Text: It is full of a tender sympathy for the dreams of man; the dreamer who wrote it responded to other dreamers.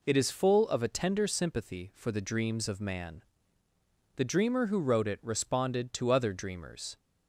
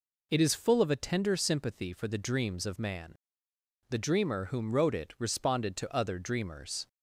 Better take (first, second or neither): first